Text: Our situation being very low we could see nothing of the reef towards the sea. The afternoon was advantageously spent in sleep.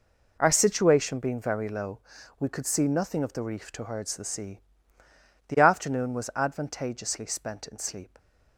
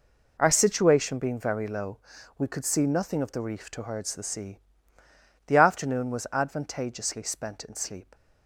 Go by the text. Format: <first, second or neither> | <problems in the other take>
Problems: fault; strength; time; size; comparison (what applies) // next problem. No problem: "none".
neither | pauses between "low" and "we"; the same in both